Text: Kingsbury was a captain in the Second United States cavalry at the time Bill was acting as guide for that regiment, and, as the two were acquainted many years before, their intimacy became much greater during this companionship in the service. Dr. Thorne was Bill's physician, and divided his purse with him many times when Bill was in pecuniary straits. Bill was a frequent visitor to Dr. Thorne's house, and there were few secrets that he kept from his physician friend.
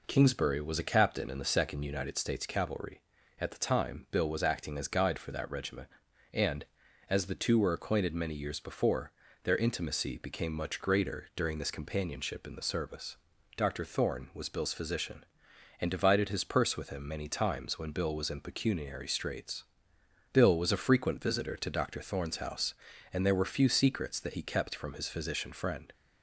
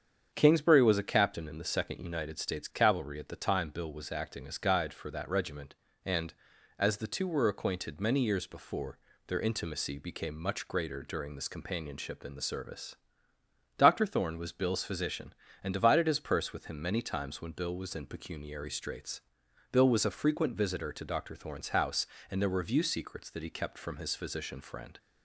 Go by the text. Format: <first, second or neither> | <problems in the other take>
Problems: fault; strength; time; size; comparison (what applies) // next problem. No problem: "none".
first | starts louder than the rest; strong; until 1.3 s; 7.5 dB // says "view" for "few"; at 22.6 s